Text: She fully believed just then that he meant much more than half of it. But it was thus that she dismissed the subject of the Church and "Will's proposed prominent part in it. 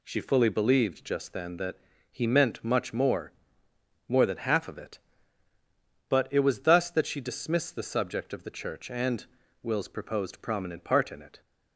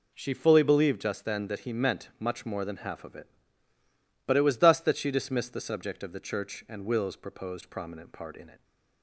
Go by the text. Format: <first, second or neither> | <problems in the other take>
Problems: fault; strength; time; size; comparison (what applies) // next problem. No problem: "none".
second | pauses between "that" and "he"; slight; at 1.7 s; 0.34 s long // says "more" twice; at 4.0 s // pauses between "and" and "Will's"; at 9.2 s; 0.38 s long